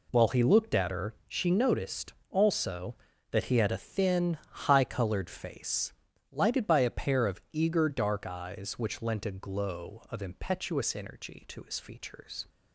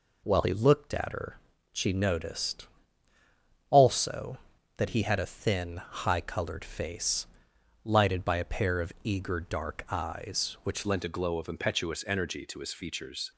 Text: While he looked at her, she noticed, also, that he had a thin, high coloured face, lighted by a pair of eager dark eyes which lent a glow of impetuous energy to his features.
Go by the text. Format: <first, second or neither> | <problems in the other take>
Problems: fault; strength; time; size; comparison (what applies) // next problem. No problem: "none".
first | changes voice at "lent"; from 10.8 s on; 2.5 s long